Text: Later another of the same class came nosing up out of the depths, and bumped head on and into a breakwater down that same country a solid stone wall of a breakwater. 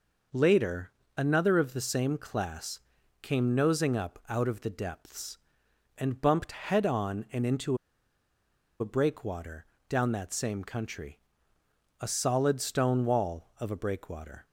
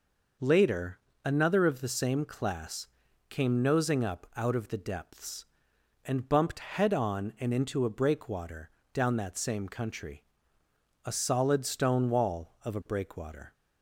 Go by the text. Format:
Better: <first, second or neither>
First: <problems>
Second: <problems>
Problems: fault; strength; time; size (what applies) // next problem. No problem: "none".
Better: second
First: pauses between "Later" and "another"; slight; at 0.9 s; 0.24 s long // pauses between "class" and "came"; at 2.7 s; 0.44 s long // pauses between "into" and "a"; at 7.7 s; 1.0 s long // pauses between "breakwater" and "down"; slight; at 9.6 s; 0.24 s long // pauses between "country" and "a"; noticeable; at 11.1 s; 0.80 s long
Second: pauses between "Later" and "another"; slight; at 0.9 s; 0.24 s long // pauses between "class" and "came"; at 2.8 s; 0.44 s long // pauses between "breakwater" and "down"; slight; at 8.6 s; 0.24 s long // pauses between "country" and "a"; noticeable; at 10.2 s; 0.80 s long